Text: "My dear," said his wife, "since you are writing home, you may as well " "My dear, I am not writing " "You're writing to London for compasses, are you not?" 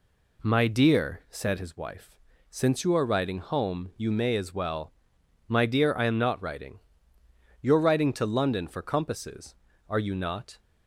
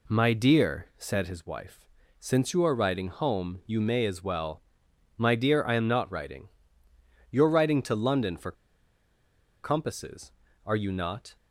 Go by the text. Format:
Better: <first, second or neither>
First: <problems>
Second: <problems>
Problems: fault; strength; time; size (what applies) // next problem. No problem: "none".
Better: first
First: none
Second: pauses between "for" and "compasses"; at 8.5 s; 1.1 s long